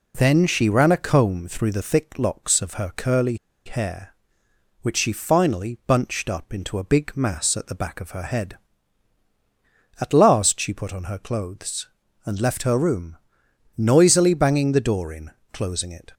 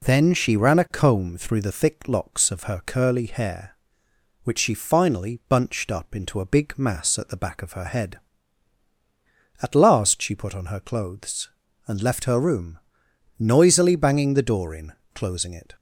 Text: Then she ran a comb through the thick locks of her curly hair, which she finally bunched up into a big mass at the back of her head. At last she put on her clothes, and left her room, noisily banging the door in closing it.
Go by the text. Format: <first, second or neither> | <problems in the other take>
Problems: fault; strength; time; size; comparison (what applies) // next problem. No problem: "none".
second | pauses between "curly" and "hair"; slight; at 3.3 s; 0.30 s long // pauses between "in" and "closing"; slight; at 15.3 s; 0.22 s long; slight in the second